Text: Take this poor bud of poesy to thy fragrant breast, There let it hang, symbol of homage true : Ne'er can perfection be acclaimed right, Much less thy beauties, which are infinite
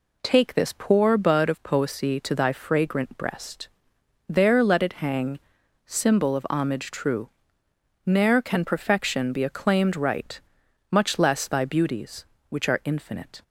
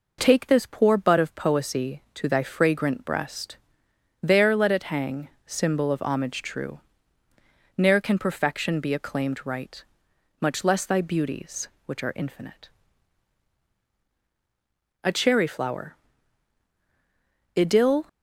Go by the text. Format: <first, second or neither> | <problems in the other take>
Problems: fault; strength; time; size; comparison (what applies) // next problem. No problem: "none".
first | goes on to say "A Cherry Flower Idyll"; strong; from 15.0 s on; 3.0 s long